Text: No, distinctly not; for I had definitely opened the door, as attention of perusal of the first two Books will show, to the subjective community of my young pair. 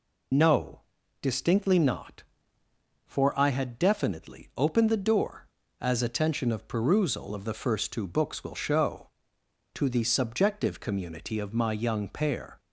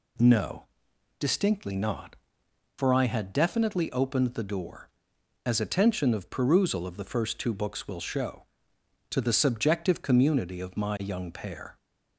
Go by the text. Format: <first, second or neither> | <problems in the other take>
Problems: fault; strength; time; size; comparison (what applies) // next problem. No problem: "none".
second | loses the start of "No"; at 0.3 s; 50 ms